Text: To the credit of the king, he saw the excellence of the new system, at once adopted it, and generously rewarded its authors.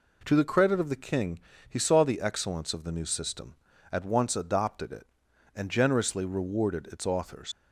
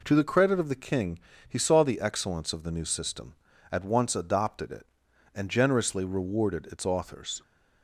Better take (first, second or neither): second